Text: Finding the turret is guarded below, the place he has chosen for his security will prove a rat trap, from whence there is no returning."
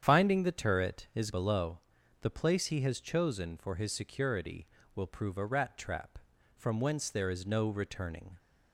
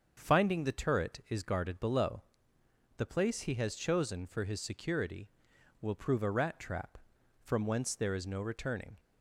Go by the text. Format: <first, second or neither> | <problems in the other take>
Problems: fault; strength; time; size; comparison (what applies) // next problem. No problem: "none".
second | starts louder than the rest; until 1.1 s; 7 dB; also in the second // skips "guarded"; at 1.3 s